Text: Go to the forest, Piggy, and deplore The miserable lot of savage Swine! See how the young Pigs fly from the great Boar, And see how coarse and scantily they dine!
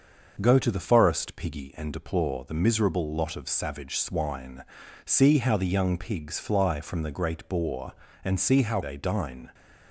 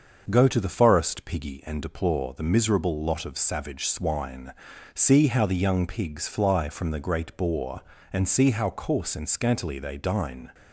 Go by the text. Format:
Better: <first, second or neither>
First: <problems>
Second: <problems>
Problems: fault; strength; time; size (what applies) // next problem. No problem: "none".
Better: second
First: starts louder than the rest; until 1.4 s; 6.5 dB // skips "coarse and scantily"; at 8.8 s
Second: starts louder than the rest; until 1.3 s; 6.5 dB